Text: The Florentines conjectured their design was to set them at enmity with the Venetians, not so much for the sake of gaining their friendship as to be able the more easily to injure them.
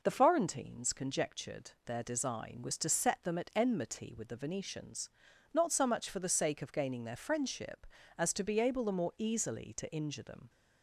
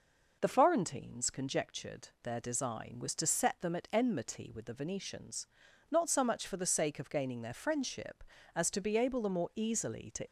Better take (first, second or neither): first